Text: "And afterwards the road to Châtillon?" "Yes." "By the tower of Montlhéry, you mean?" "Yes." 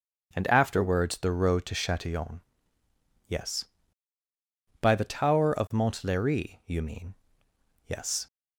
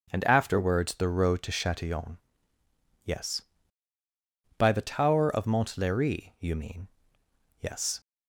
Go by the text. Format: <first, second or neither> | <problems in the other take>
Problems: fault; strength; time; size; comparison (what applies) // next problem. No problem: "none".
neither | starts louder than the rest; the same in both